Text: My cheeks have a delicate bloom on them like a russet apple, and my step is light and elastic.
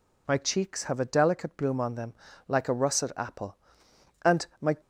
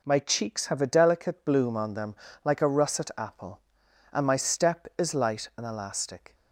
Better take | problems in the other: second | pauses between "them" and "like"; slight; at 2.1 s; 0.34 s long; slight in the second // pauses between "and" and "my"; slight; at 4.4 s; 0.16 s long // stops before "step is light and elastic"; at 4.7 s

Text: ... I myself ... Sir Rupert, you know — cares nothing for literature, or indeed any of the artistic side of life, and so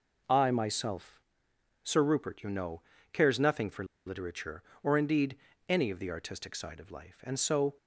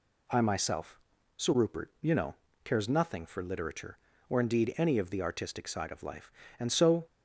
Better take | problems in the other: second | pauses between "for" and "literature"; slight; at 3.8 s; 0.22 s long // pauses between "indeed" and "any"; slight; at 5.3 s; 0.32 s long

